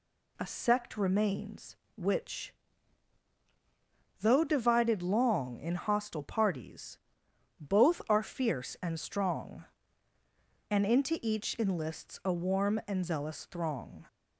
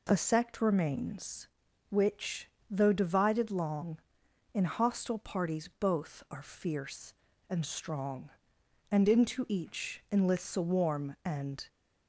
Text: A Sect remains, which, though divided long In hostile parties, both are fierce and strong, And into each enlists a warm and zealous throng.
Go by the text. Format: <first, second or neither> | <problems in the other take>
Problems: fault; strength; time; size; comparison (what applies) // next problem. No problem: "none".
first | pauses between "each" and "enlists"; slight; at 10.0 s; 0.22 s long // stops before "zealous throng"; at 11.6 s